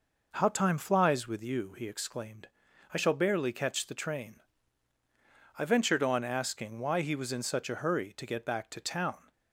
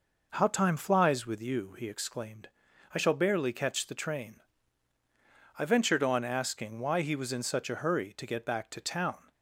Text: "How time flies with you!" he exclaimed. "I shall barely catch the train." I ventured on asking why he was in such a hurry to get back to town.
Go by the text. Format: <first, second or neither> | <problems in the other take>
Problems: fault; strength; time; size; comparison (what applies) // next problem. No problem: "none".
neither | none